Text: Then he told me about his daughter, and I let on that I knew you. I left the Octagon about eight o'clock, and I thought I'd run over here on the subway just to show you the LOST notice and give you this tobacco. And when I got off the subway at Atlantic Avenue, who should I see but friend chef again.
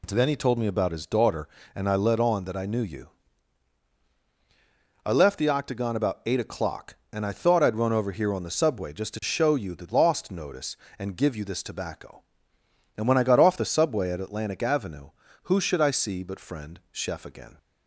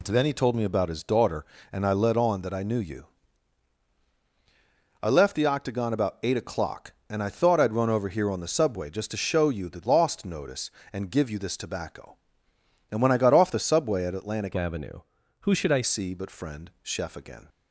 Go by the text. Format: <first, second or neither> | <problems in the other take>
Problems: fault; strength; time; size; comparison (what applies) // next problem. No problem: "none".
first | changes voice from "Avenue" to "I"; from 14.5 to 15.8 s; 1.3 s long